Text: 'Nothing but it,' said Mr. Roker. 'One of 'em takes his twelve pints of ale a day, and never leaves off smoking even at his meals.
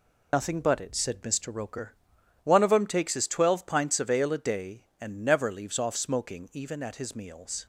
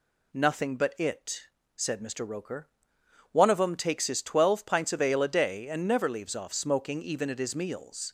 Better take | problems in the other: second | loses the start of "Nothing"; at 0.3 s; 125 ms

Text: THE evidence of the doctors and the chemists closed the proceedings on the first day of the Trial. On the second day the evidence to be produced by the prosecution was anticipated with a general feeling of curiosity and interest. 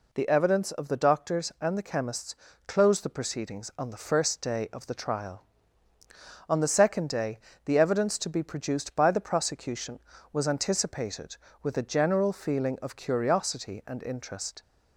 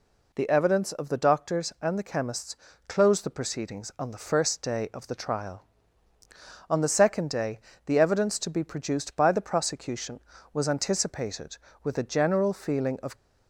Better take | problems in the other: first | pauses between "chemists" and "closed"; slight; at 2.5 s; 0.32 s long; slight in the first // pauses between "day" and "the"; slight; at 7.6 s; 0.24 s long; slight in the first // stops before "curiosity and interest"; at 13.1 s

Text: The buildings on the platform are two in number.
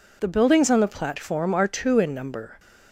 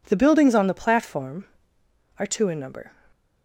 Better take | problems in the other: neither | none

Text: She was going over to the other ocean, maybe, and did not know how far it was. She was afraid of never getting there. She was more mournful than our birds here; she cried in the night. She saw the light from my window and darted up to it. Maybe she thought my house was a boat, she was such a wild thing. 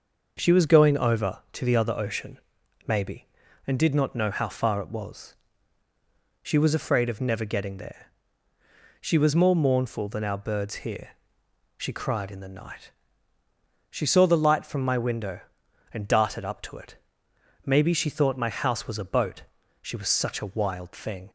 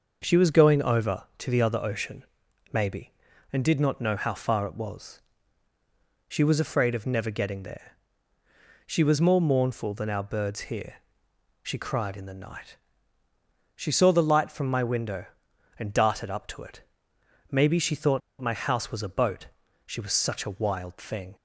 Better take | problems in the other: first | starts louder than the rest; noticeable; until 1.2 s; 6 dB; noticeable in the first // pauses between "thought" and "my"; slight; at 18.2 s; 0.21 s long

